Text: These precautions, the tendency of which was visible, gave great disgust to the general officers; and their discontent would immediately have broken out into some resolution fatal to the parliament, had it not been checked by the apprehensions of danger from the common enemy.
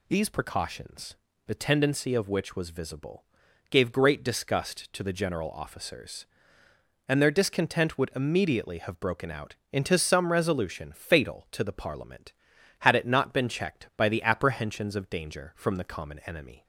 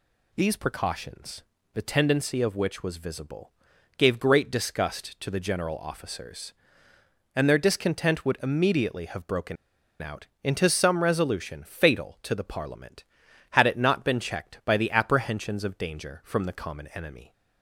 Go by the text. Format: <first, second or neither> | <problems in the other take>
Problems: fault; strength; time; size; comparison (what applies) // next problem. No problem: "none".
first | pauses between "broken" and "out"; noticeable; at 9.5 s; 0.46 s long // pauses between "out" and "into"; slight; at 10.2 s; 0.18 s long; slight in the first